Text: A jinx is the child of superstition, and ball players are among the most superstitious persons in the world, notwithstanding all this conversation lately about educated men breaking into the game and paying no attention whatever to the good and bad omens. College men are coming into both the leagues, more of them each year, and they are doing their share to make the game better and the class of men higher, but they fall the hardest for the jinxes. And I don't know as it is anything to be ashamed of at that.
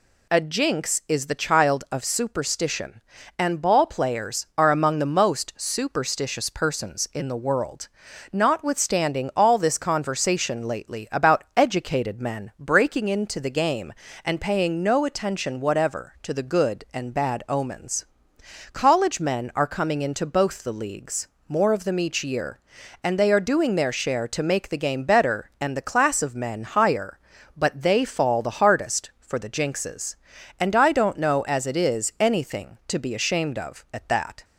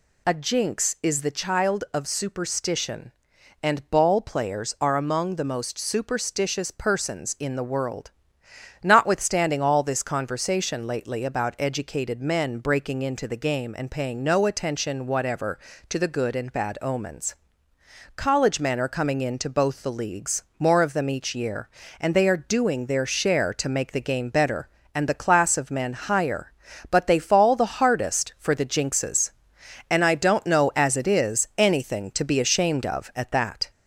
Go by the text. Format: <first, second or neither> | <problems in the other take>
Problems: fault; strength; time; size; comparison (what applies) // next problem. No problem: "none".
first | gets louder; slight; throughout; 2.5 dB